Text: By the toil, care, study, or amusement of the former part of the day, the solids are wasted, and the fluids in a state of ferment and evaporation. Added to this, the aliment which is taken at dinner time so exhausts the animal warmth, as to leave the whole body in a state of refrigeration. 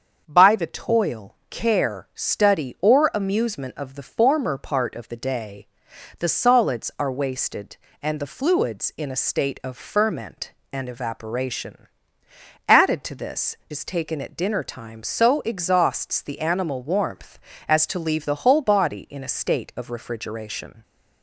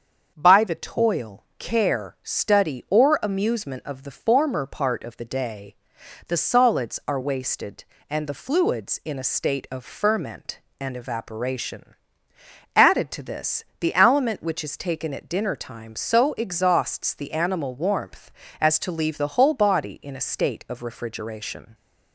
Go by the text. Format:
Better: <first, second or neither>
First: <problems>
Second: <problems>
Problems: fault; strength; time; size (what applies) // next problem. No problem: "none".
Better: second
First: starts louder than the rest; until 1.2 s; 7 dB // skips "the aliment which"; at 13.6 s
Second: starts louder than the rest; until 1.3 s; 7 dB